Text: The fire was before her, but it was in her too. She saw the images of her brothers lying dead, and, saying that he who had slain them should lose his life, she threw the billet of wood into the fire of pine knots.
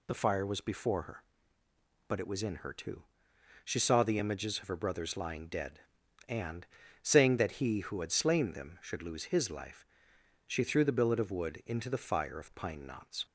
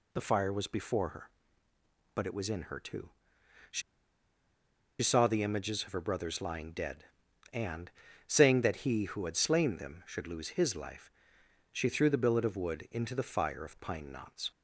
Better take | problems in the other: first | pauses between "She" and "saw"; at 3.8 s; 1.2 s long

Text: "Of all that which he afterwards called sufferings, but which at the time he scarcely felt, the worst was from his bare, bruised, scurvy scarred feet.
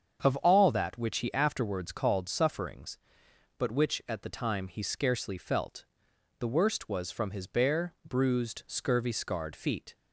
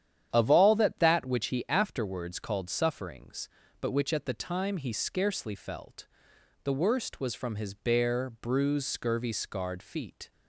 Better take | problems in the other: first | starts louder than the rest; strong; until 1.3 s; 9.5 dB; strong in the first // says "that" twice; at 0.9 s

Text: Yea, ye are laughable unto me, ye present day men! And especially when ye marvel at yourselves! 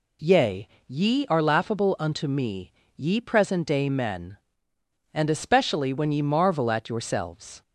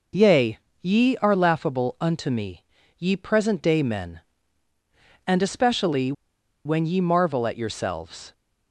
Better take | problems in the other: first | pauses between "especially" and "when"; noticeable; at 6.1 s; 0.53 s long

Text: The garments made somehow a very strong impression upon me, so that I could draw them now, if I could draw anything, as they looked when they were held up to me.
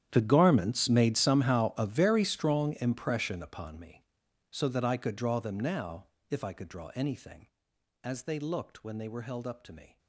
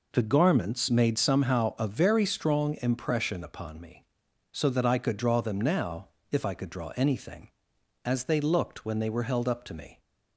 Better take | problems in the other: second | gets quieter; strong; throughout; 19 dB

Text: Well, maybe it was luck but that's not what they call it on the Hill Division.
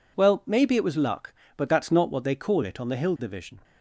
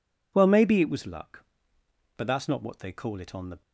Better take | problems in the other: first | stops before "Hill Division"; at 3.6 s

